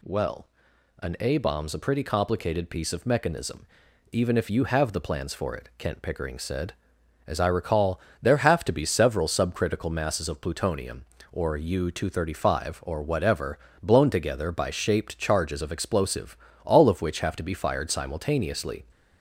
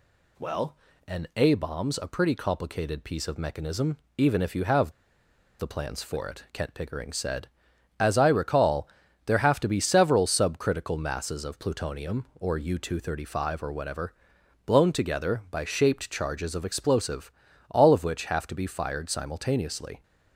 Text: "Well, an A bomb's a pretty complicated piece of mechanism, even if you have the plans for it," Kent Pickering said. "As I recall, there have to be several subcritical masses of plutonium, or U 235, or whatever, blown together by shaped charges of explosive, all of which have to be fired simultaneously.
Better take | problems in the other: first | pauses between "have" and "the"; noticeable; at 4.9 s; 0.68 s long

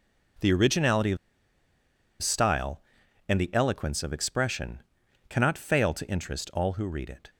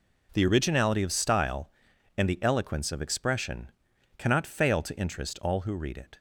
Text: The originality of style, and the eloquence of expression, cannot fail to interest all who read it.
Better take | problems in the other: second | pauses between "of" and "style"; at 1.1 s; 1.0 s long

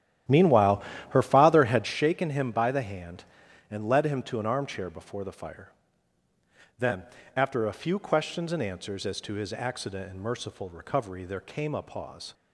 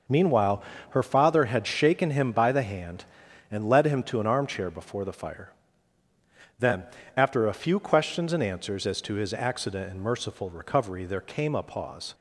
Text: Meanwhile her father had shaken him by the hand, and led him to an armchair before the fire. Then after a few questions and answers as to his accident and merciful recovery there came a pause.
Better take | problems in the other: second | starts louder than the rest; strong; until 1.9 s; 11.5 dB // pauses between "Meanwhile" and "her"; slight; at 0.8 s; 0.28 s long; slight in the second // pauses between "Then" and "after"; slight; at 7.0 s; 0.32 s long; slight in the second

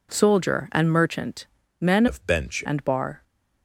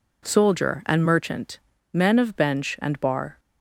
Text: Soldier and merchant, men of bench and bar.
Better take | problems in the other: second | changes voice from "of" to "bench"; from 2.0 to 2.6 s; 0.6 s long

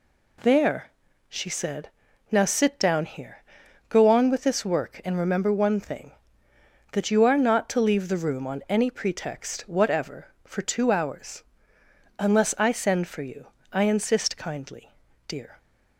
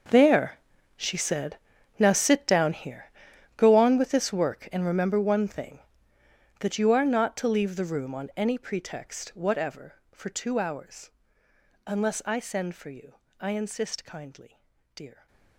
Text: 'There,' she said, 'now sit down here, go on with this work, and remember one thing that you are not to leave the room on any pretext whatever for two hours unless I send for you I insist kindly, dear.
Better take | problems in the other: first | gets quieter; strong; throughout; 16.5 dB // pauses between "hours" and "unless"; noticeable; at 11.1 s; 0.76 s long; noticeable in the first // pauses between "you" and "I"; slight; at 13.1 s; 0.24 s long; slight in the first

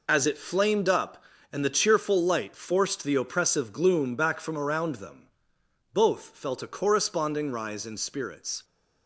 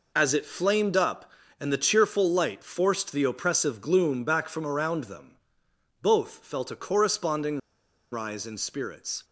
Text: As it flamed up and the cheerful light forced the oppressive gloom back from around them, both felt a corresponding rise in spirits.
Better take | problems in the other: first | pauses between "corresponding" and "rise"; noticeable; at 7.5 s; 0.52 s long

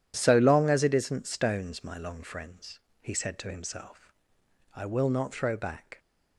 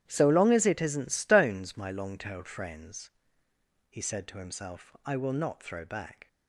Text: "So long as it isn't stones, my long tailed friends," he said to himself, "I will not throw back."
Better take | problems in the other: second | starts louder than the rest; strong; until 1.1 s; 10.5 dB; strong in the second // skips "tailed"; at 2.2 s

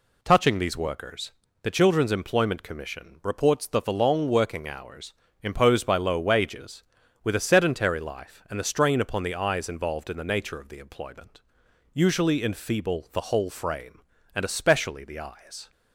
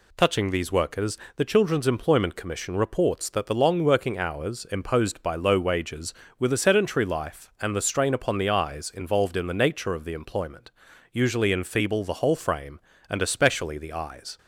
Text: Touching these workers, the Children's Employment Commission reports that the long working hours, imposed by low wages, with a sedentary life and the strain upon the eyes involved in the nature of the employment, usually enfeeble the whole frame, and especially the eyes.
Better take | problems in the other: neither | none

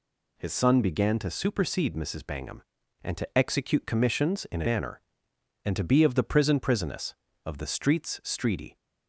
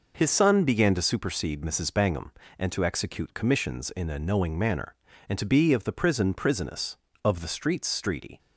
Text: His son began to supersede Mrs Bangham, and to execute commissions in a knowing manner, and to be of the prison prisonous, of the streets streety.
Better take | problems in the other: second | skips "knowing"; at 4.6 s

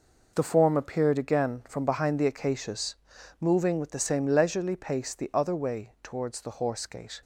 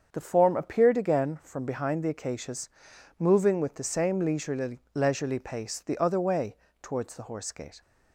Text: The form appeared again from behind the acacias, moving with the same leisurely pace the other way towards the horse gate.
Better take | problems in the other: first | starts louder than the rest; strong; until 1.1 s; 7 dB // says "leisurely" twice; at 4.9 s // pauses between "way" and "towards"; slight; at 6.5 s; 0.26 s long

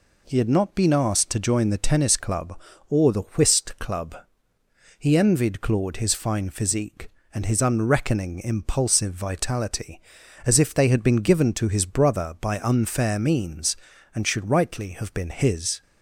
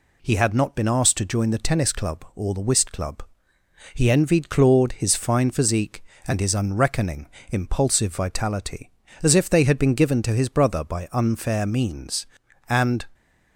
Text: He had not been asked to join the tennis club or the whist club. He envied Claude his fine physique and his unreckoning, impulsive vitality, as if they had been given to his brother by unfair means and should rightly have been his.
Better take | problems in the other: first | stops before "should rightly have been his"; at 13.1 s

